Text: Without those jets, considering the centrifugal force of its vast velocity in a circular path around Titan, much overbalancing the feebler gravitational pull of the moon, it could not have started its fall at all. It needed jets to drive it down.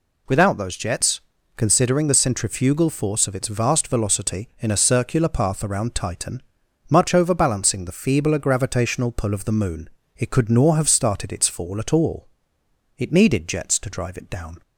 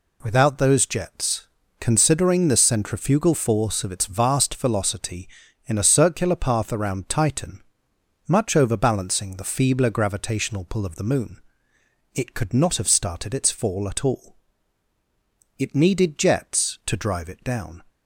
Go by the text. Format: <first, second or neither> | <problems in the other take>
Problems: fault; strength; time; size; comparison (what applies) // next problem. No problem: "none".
second | says "nor" for "not"; at 10.4 s